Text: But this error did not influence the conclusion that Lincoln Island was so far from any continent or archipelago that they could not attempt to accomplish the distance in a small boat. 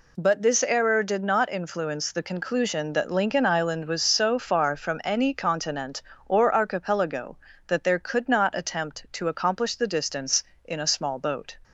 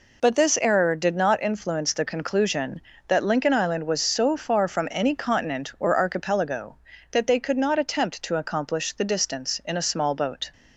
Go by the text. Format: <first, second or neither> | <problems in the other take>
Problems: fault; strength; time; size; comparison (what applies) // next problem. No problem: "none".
second | says "there" for "they"; at 7.8 s